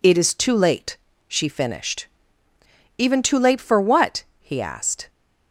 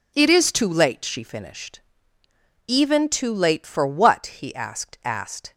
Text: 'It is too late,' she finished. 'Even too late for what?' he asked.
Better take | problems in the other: first | says "asked" twice; at 5.0 s

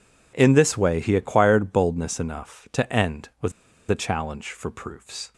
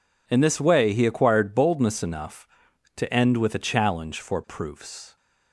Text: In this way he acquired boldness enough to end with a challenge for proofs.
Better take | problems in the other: second | pauses between "with" and "a"; at 3.5 s; 0.38 s long

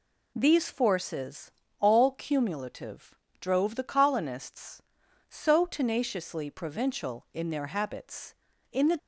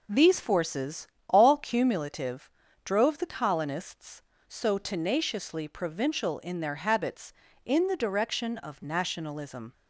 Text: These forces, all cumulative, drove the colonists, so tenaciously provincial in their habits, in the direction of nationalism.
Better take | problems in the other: second | stops before "direction of nationalism"; at 8.9 s

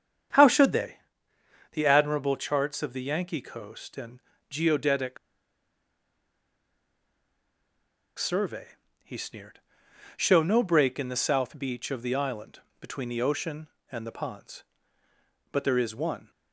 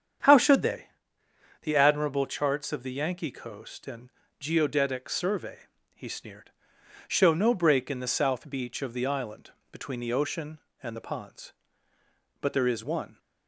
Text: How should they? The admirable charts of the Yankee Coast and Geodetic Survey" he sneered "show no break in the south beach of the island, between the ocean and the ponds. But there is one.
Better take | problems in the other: second | starts louder than the rest; strong; until 2.1 s; 8 dB; strong in the second // pauses between "and" and "Geodetic"; slight; at 4.1 s; 0.30 s long; slight in the second // pauses between "Geodetic" and "Survey"; strong; at 5.1 s; 3.0 s long // pauses between "Survey" and "he"; slight; at 8.7 s; 0.34 s long; slight in the second // pauses between "sneered" and "show"; noticeable; at 9.6 s; 0.56 s long; noticeable in the second

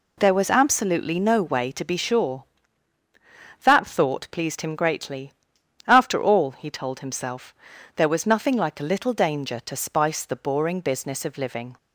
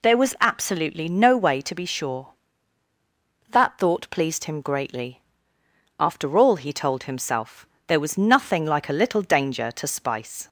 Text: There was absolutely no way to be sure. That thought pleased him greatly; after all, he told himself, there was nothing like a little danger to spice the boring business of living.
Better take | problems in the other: first | stops before "the boring business of living"; at 10.4 s

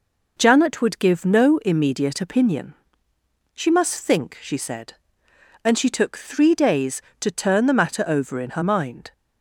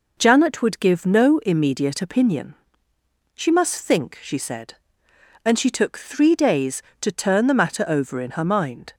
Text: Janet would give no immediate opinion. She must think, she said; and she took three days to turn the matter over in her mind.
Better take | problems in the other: neither | none

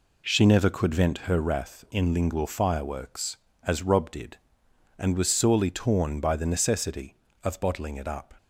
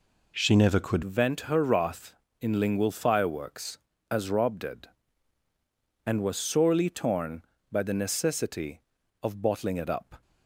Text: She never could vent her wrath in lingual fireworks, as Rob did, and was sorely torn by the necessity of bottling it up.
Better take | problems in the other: first | changes voice at "vent"; from 1.0 s on; 9.2 s long

